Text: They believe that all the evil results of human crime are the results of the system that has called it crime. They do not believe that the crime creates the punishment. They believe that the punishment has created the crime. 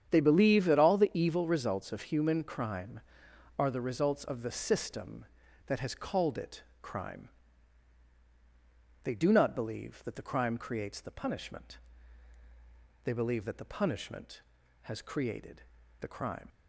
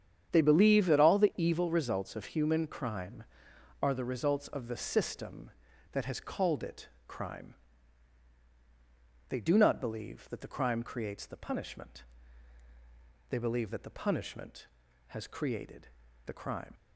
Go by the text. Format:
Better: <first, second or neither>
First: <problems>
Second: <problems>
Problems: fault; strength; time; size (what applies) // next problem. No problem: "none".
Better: neither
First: starts louder than the rest; strong; until 1.1 s; 8.5 dB // pauses between "it" and "crime"; slight; at 6.6 s; 0.20 s long // pauses between "created" and "the"; at 15.6 s; 0.38 s long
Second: starts louder than the rest; strong; until 1.3 s; 8.5 dB // pauses between "it" and "crime"; slight; at 6.8 s; 0.20 s long // pauses between "created" and "the"; at 15.8 s; 0.38 s long